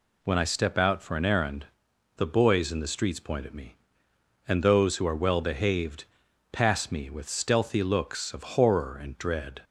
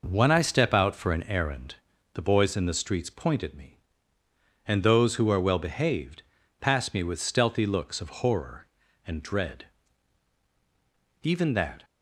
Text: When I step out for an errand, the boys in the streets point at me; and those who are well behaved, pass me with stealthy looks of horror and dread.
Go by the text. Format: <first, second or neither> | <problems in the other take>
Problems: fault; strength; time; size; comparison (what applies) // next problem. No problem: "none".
first | goes on to say "Even that"; noticeable; from 11.2 s on; 0.62 s long